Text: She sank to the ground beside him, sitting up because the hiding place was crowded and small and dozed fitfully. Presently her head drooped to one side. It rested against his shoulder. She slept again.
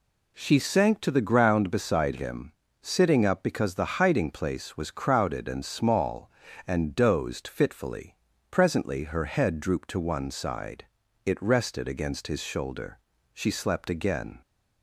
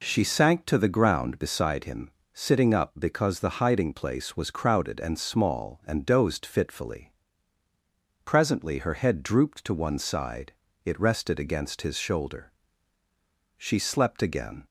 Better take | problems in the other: neither | none

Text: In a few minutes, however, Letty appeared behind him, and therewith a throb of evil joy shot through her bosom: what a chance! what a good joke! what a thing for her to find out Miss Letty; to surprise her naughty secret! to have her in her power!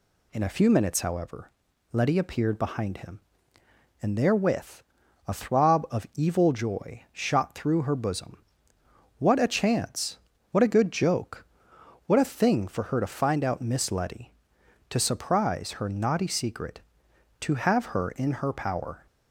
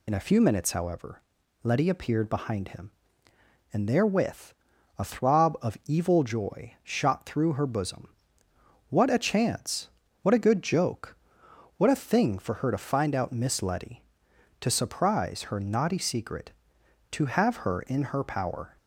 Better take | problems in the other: first | loses the start of "In"; at 0.0 s; 50 ms // pauses between "therewith" and "a"; at 4.5 s; 0.44 s long; also in the first

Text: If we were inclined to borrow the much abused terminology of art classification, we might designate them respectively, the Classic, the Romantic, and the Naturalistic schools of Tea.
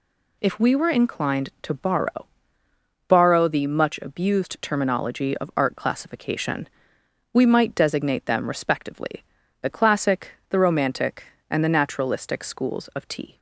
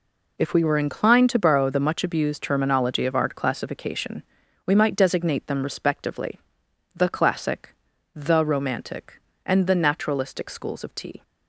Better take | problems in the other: second | says "borrow" twice; at 3.0 s

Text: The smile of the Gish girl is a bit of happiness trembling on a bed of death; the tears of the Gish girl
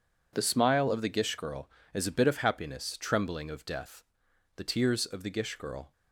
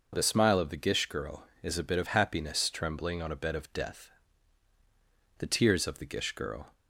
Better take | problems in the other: second | skips "on a bed"; at 3.4 s

